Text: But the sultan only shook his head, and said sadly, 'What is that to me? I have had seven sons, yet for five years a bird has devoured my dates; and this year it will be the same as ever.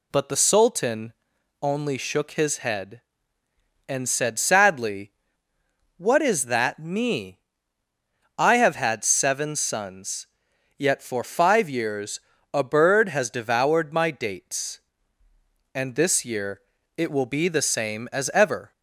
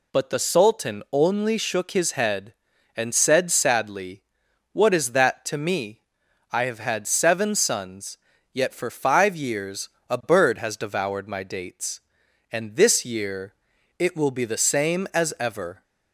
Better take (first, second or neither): second